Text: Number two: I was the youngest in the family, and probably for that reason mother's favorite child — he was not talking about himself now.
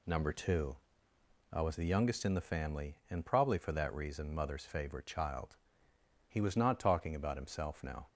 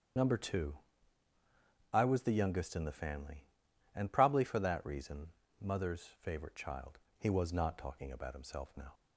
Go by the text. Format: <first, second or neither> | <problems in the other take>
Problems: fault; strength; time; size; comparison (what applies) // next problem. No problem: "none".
first | loses the start of "Number"; at 0.1 s; 50 ms // starts louder than the rest; strong; until 2.3 s; 8 dB // pauses between "reason" and "mother's"; slight; at 5.2 s; 0.30 s long